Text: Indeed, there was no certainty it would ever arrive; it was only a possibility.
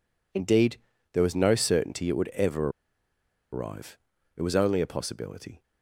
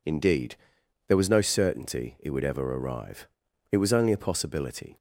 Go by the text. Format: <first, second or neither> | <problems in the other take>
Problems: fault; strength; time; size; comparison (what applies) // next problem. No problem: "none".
second | pauses between "ever" and "arrive"; noticeable; at 2.6 s; 0.83 s long